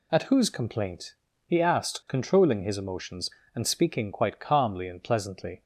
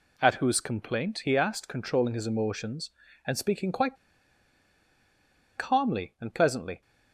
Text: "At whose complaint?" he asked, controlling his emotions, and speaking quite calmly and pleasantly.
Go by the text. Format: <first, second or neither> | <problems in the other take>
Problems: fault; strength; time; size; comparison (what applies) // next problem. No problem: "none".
first | pauses between "quite" and "calmly"; strong; at 3.9 s; 1.6 s long